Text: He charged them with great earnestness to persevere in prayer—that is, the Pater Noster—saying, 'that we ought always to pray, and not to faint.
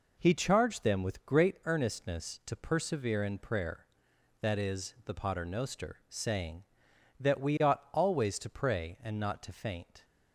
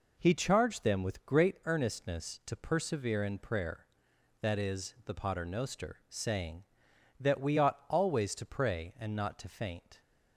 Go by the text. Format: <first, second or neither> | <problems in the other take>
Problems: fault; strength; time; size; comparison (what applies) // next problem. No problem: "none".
neither | none